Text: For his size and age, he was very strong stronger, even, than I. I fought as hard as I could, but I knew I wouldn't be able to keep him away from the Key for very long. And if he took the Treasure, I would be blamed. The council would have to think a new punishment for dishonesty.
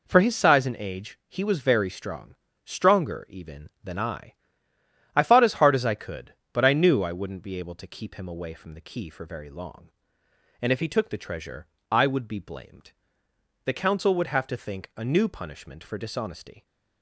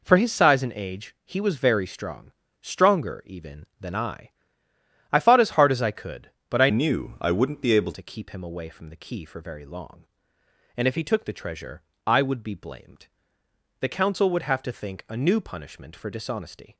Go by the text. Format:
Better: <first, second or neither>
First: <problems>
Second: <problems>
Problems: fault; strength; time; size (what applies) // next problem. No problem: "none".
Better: first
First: pauses between "strong" and "stronger"; slight; at 2.3 s; 0.28 s long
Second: pauses between "strong" and "stronger"; slight; at 2.3 s; 0.28 s long // changes voice from "knew" to "able"; from 6.6 to 7.9 s; 1.3 s long